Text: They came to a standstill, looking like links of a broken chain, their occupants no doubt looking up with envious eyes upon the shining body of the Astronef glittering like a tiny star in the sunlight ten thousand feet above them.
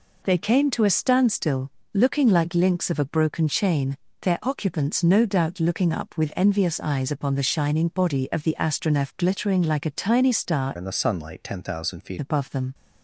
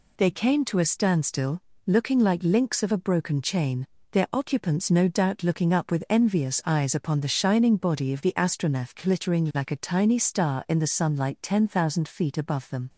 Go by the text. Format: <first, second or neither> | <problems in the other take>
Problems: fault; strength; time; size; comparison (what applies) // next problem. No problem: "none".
second | changes voice from "in" to "feet"; from 10.7 to 12.1 s; 1.4 s long